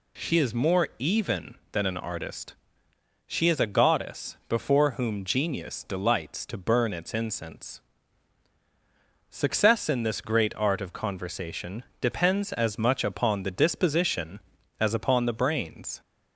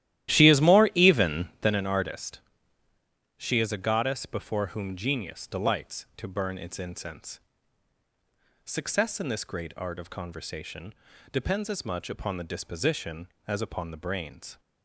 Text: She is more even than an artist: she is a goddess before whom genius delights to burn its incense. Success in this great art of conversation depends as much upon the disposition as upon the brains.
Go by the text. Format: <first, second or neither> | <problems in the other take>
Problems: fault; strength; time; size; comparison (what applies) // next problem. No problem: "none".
first | starts louder than the rest; strong; until 1.7 s; 13.5 dB // pauses between "conversation" and "depends"; at 10.9 s; 0.38 s long; slight in the first